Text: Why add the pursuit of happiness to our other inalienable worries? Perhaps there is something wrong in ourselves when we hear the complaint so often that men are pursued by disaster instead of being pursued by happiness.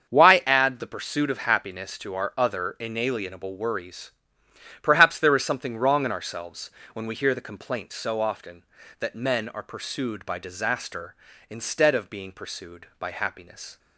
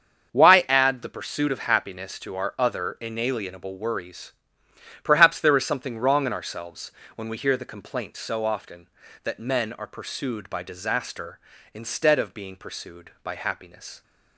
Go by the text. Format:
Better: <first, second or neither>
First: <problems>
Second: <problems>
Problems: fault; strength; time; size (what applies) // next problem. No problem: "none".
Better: neither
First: starts louder than the rest; until 1.1 s; 7 dB // pauses between "ourselves" and "when"; slight; at 6.6 s; 0.24 s long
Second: starts louder than the rest; until 1.3 s; 7 dB // pauses between "ourselves" and "when"; slight; at 6.9 s; 0.24 s long